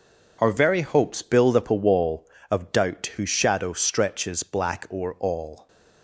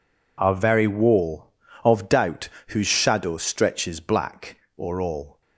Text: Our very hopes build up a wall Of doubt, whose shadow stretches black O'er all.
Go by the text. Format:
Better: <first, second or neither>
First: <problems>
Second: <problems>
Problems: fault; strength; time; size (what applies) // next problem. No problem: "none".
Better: first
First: none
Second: skips "hopes build up a"; at 0.8 s // pauses between "black" and "O'er"; slight; at 4.5 s; 0.22 s long